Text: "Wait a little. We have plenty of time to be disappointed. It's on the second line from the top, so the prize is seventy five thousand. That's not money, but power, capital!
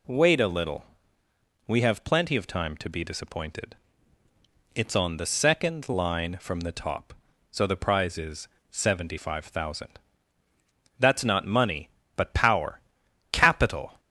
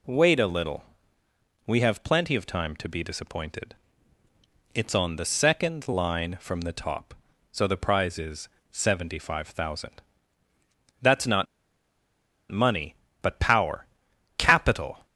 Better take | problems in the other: first | pauses between "is" and "seventy"; slight; at 8.4 s; 0.20 s long; slight in the first // pauses between "not" and "money"; at 11.4 s; 1.0 s long

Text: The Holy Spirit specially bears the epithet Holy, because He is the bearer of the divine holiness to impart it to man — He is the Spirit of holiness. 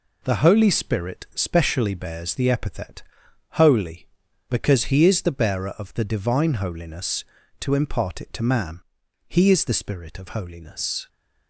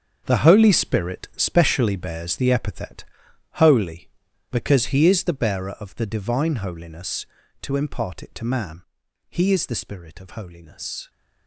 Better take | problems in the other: first | gets quieter; strong; throughout; 12.5 dB // pauses between "epithet" and "Holy"; noticeable; at 3.0 s; 0.54 s long; noticeable in the first

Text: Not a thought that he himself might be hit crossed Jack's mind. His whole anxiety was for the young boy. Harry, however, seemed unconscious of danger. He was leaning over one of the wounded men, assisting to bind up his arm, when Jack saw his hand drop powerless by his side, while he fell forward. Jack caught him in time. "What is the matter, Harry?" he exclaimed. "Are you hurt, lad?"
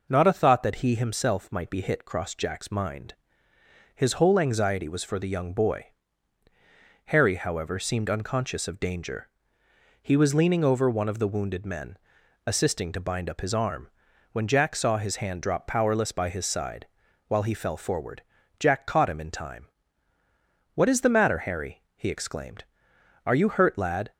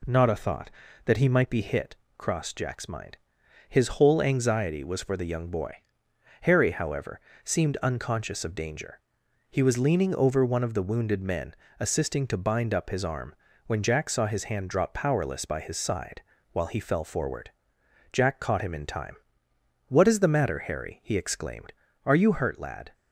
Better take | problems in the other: first | skips "himself"; at 1.2 s // pauses between "hit" and "crossed"; slight; at 1.9 s; 0.22 s long

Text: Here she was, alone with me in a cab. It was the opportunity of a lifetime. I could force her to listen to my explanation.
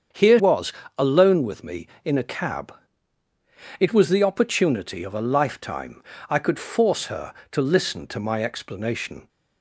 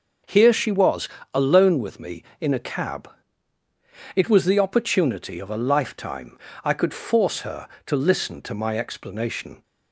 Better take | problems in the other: second | starts louder than the rest; strong; until 1.3 s; 7.5 dB // skips "she"; at 0.3 s

